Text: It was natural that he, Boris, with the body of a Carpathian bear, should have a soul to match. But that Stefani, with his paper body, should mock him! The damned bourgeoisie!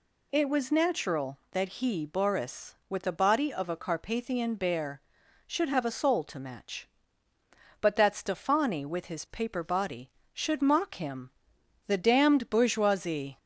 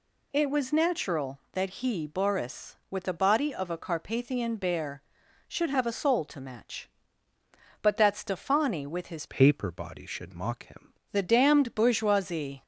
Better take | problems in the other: first | changes voice from "paper" to "him"; from 9.2 to 10.9 s; 1.7 s long

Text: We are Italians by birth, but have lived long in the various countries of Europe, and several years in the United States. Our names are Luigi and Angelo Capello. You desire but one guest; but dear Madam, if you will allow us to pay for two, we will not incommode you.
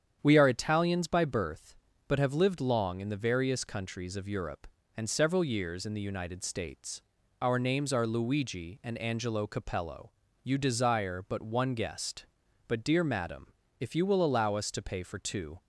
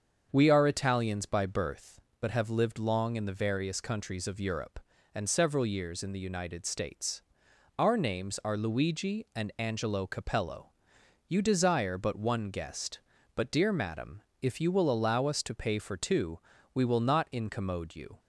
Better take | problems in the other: second | starts louder than the rest; strong; until 1.2 s; 8.5 dB; also in the second // stops before "we will not incommode you"; at 15.5 s

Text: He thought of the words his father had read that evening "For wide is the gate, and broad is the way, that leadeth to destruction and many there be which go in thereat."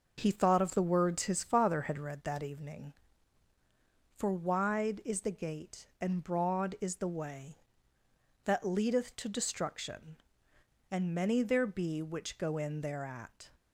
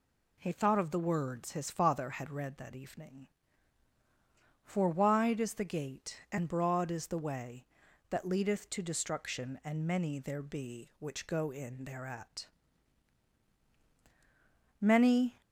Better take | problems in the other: first | goes on to say "Many"; noticeable; from 14.7 s on; 0.62 s long

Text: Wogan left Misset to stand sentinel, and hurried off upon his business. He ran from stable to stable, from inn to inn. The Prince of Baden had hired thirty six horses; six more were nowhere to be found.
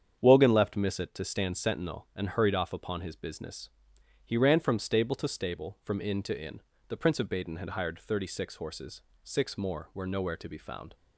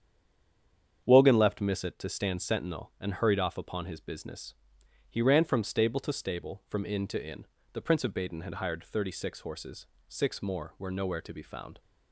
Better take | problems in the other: first | stays silent before the first word; until 1.0 s; 1.0 s long // starts louder than the rest; strong; until 2.0 s; 8 dB; strong in the first

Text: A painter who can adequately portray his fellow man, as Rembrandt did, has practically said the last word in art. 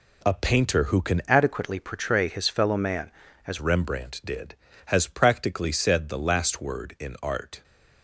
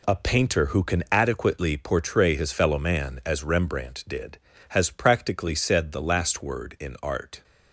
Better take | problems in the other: second | changes voice from "adequately" to "as"; from 1.2 to 3.5 s; 2.3 s long

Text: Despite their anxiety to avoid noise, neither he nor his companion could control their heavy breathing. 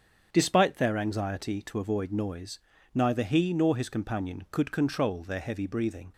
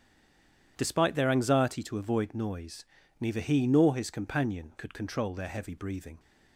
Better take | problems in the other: first | stays silent before the first word; slight; until 0.7 s; 0.7 s long // starts louder than the rest; strong; until 1.7 s; 10 dB; strong in the first

